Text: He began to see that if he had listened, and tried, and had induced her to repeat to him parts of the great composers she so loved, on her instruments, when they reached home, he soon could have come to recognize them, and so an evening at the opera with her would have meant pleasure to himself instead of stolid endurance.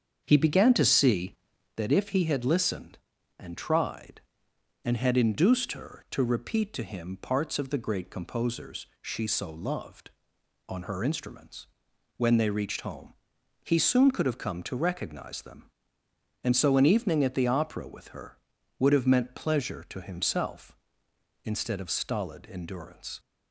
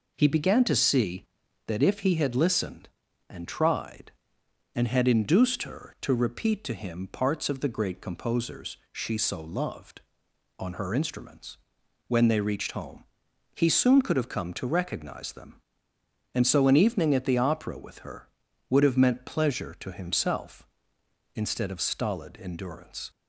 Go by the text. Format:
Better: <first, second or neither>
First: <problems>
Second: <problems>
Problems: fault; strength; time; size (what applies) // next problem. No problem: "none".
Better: second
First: starts louder than the rest; strong; until 1.8 s; 7.5 dB // pauses between "composers" and "she"; slight; at 8.8 s; 0.16 s long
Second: pauses between "composers" and "she"; slight; at 8.7 s; 0.16 s long